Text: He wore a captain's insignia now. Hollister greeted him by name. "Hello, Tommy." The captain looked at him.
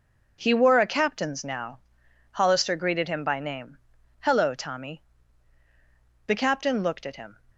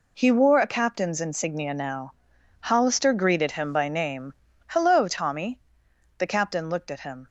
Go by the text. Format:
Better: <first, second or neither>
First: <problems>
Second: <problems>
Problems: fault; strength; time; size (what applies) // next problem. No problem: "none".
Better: second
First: skips "insignia"; at 1.4 s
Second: none